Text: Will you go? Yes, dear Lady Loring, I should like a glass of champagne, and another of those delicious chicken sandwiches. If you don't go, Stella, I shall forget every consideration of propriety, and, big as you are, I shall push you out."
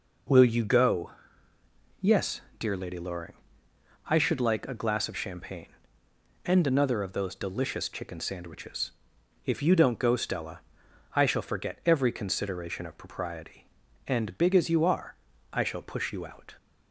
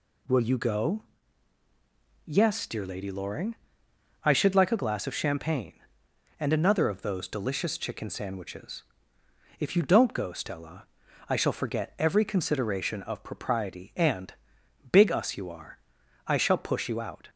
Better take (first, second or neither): first